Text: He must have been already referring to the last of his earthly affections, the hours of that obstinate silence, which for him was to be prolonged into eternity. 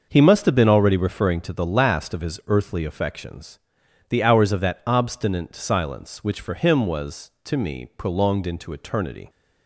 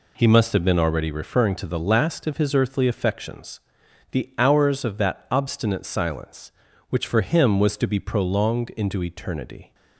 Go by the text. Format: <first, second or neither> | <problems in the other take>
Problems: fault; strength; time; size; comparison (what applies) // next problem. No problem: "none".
second | starts louder than the rest; until 1.0 s; 6 dB // says "me" for "be"; at 7.5 s